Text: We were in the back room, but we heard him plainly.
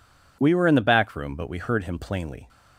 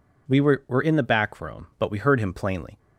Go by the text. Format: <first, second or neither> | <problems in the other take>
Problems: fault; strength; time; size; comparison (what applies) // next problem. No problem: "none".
first | says "were" twice; at 0.6 s